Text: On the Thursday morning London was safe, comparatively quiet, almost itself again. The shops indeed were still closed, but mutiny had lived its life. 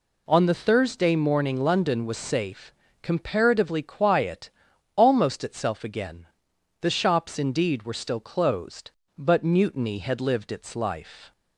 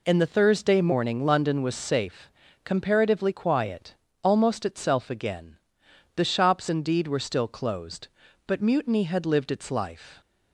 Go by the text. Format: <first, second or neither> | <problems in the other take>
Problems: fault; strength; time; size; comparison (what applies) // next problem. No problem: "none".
first | says "In" for "On"; at 0.0 s